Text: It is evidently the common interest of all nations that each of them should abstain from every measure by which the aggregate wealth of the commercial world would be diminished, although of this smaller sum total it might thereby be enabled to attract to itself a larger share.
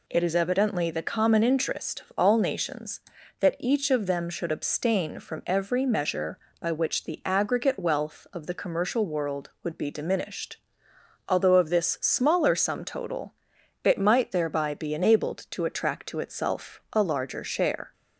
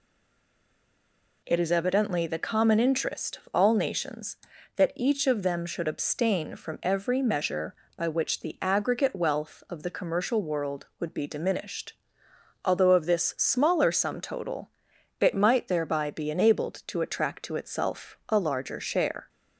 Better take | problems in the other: first | stays silent before the first word; noticeable; until 1.4 s; 1.4 s long // pauses between "total" and "it"; noticeable; at 14.7 s; 0.48 s long; noticeable in the first

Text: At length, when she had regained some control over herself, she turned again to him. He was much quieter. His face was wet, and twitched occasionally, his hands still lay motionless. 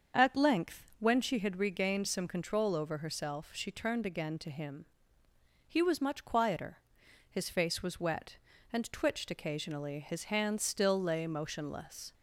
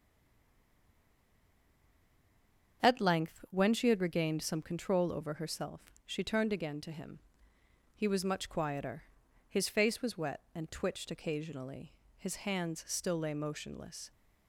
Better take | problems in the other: first | stays silent before the first word; strong; until 2.8 s; 2.8 s long // starts louder than the rest; strong; until 3.8 s; 7 dB; also in the first

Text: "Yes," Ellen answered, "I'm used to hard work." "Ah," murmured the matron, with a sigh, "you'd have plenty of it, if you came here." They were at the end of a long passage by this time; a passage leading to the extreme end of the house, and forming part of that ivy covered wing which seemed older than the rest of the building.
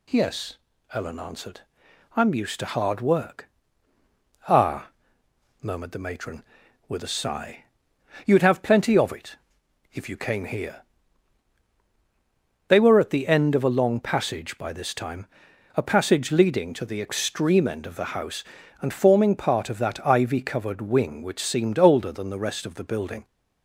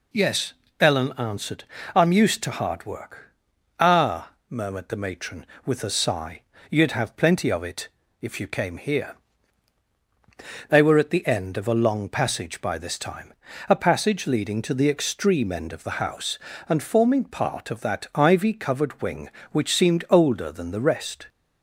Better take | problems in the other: first | stops before "of the building"; at 21.2 s

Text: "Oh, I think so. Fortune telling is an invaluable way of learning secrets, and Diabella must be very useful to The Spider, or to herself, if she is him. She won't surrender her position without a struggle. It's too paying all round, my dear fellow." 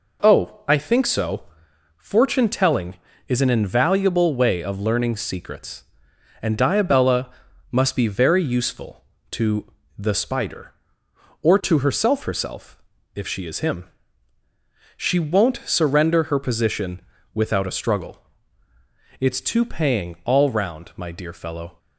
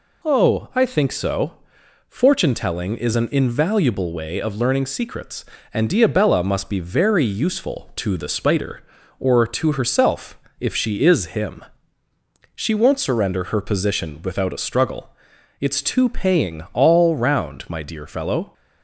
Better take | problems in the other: second | pauses between "Diabella" and "must"; at 7.2 s; 0.42 s long // pauses between "to" and "The"; slight; at 9.7 s; 0.26 s long // says "herself" twice; at 12.2 s // pauses between "position" and "without"; slight; at 17.0 s; 0.32 s long

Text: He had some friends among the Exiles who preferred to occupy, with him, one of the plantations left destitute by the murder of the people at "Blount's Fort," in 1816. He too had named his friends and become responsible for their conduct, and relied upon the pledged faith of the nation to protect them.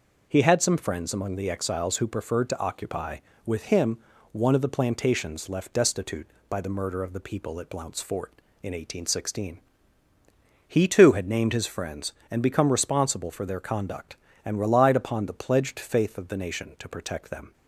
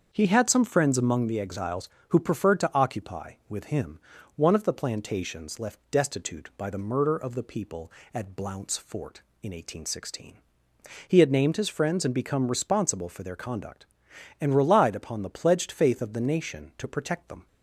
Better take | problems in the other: first | starts louder than the rest; until 1.1 s; 7 dB // skips "too"; at 11.2 s

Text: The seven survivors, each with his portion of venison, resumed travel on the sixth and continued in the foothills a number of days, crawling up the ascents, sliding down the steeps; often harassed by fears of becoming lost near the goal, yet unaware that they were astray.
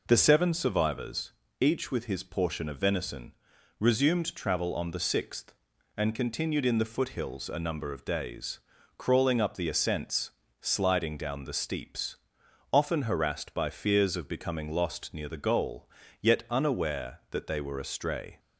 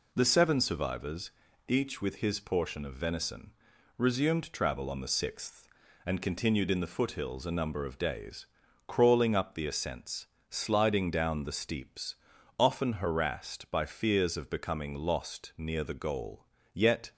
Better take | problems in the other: first | stops before "unaware that they were astray"; at 17.1 s

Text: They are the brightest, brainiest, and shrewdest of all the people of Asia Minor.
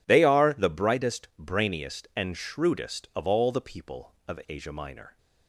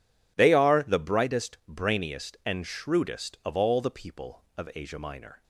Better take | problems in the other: neither | none

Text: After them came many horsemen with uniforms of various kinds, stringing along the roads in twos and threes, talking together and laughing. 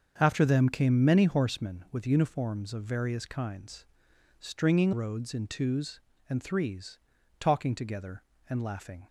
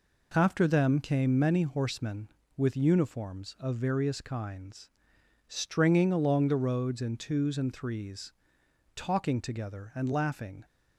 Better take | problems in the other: second | starts louder than the rest; until 1.1 s; 7 dB // skips "along the"; at 4.9 s

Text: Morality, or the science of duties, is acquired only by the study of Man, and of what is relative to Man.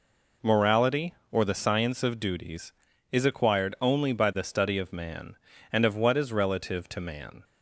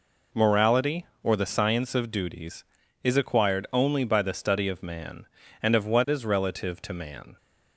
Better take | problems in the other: neither | none

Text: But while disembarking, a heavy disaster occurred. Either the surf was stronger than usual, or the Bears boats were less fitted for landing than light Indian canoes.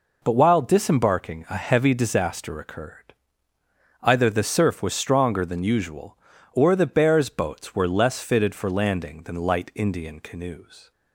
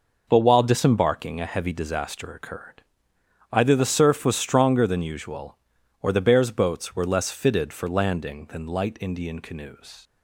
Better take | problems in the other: neither | none

